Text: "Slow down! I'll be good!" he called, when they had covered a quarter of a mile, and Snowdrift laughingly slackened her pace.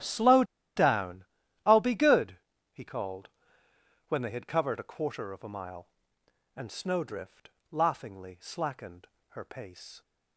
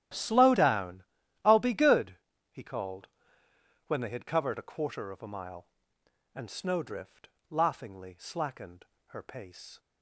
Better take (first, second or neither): second